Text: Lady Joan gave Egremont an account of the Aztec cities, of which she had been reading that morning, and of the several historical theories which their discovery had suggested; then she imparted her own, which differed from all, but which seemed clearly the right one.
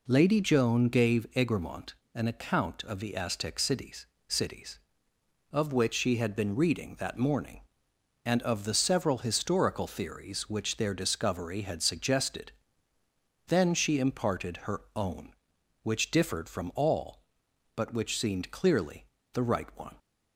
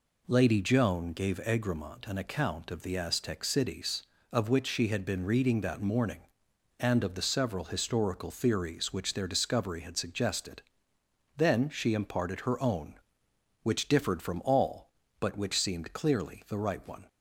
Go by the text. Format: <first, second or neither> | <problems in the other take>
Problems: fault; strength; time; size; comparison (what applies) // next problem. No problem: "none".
second | pauses between "Egremont" and "an"; slight; at 1.9 s; 0.18 s long // says "cities" twice; at 4.2 s // pauses between "her" and "own"; slight; at 14.8 s; 0.16 s long // pauses between "clearly" and "the"; slight; at 19.0 s; 0.30 s long